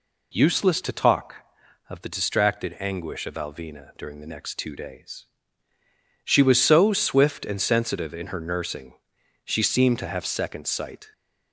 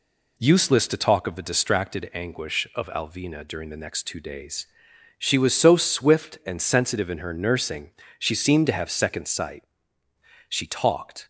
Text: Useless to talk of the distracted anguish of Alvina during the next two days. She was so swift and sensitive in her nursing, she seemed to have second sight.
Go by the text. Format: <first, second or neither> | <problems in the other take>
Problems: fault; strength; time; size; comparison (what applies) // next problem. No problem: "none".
first | goes on to say "She talked"; noticeable; from 10.4 s on; 0.80 s long